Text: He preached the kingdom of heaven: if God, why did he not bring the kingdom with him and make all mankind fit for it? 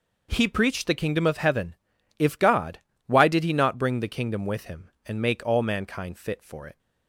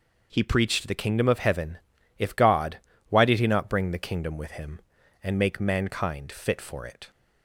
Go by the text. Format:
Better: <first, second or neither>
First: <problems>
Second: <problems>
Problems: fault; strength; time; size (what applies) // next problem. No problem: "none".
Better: first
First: none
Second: skips "all"; at 5.6 s